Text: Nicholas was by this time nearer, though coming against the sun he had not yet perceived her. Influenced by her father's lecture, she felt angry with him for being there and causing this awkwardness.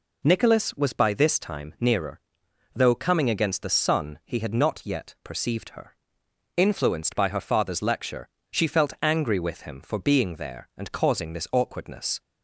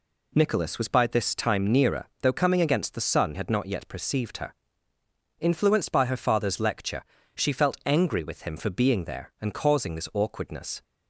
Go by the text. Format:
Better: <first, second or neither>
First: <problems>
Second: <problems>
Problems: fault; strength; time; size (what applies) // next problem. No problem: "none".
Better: first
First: none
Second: skips "he"; at 3.3 s